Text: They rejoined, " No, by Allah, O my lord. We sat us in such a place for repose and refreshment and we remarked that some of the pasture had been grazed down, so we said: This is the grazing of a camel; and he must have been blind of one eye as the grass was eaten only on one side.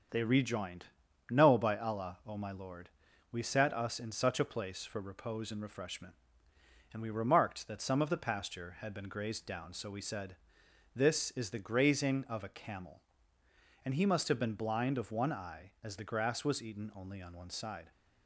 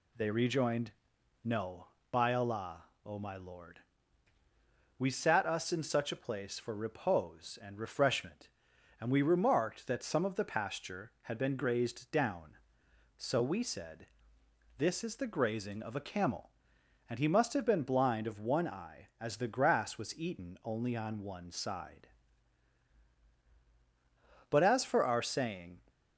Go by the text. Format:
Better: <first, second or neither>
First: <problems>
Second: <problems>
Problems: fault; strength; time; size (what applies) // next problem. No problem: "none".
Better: first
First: none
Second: goes on to say "But as for our saying"; noticeable; from 24.5 s on; 1.3 s long